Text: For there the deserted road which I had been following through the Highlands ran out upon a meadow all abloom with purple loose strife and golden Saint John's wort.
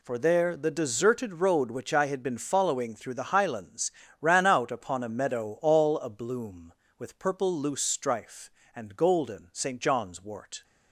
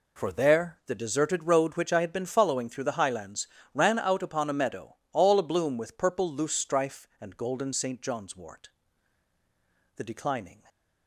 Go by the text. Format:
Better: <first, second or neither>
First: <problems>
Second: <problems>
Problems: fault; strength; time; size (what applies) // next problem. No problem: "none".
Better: first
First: pauses between "Highlands" and "ran"; slight; at 3.9 s; 0.28 s long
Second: pauses between "Highlands" and "ran"; slight; at 3.4 s; 0.28 s long // pauses between "meadow" and "all"; slight; at 4.9 s; 0.18 s long // goes on to say "The declining"; noticeable; from 9.9 s on; 0.66 s long